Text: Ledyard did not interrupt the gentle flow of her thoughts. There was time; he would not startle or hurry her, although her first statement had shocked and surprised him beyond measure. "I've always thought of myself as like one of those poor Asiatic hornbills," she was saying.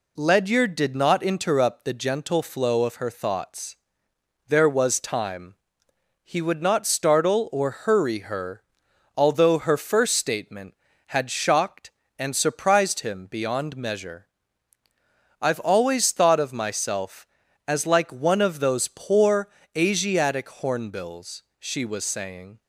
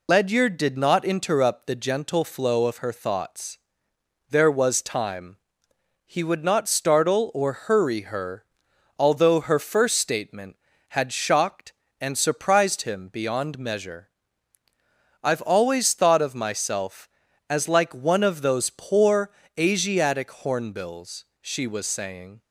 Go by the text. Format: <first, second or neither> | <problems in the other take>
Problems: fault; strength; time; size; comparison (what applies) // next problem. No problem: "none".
first | loses the start of "Ledyard"; at 0.0 s; 95 ms // pauses between "poor" and "Asiatic"; slight; at 19.3 s; 0.26 s long; slight in the first